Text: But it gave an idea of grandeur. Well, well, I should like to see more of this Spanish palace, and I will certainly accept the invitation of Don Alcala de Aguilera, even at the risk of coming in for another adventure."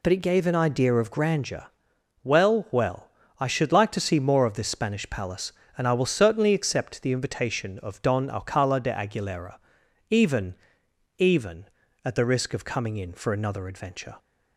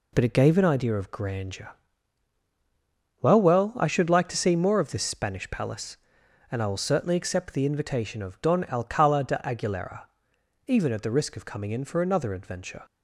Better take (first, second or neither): second